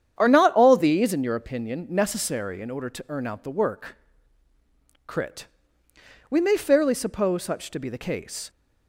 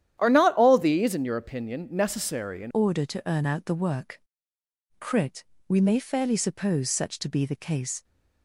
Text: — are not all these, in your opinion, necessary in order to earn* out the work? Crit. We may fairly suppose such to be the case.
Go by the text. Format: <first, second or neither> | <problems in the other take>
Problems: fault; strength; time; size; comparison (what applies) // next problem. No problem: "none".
first | starts louder than the rest; strong; until 1.2 s; 10.5 dB; strong in the first // changes voice at "order"; from 2.7 s on; 5.3 s long